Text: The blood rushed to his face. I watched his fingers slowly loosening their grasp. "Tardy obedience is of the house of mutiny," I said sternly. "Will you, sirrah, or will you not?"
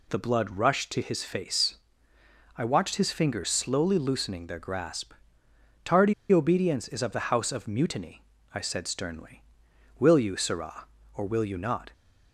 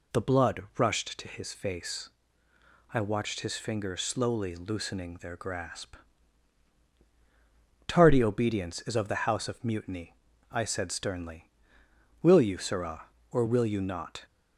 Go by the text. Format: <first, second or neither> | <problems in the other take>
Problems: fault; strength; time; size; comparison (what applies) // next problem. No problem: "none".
second | pauses between "Tardy" and "obedience"; slight; at 6.1 s; 0.18 s long